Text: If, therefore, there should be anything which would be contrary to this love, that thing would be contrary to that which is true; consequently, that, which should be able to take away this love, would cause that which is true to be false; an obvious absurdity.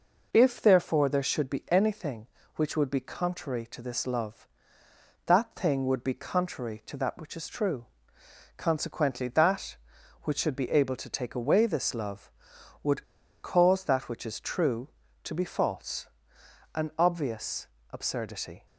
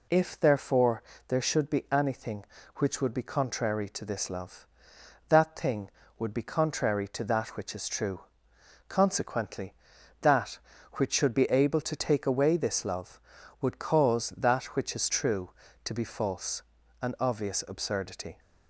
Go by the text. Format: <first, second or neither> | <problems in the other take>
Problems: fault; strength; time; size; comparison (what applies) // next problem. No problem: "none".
second | pauses between "would" and "cause"; at 13.0 s; 0.40 s long // pauses between "obvious" and "absurdity"; slight; at 17.6 s; 0.24 s long